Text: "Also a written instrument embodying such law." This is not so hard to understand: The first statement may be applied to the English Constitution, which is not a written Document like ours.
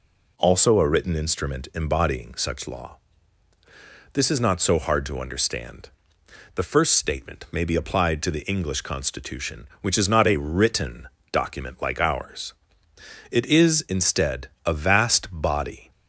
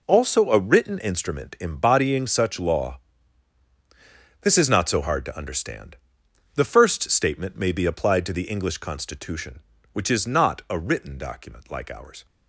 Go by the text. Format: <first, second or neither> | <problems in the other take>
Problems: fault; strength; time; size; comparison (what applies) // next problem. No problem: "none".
second | pauses between "written" and "Document"; slight; at 11.0 s; 0.24 s long // goes on to say "It is instead a vast body"; strong; from 13.2 s on; 2.6 s long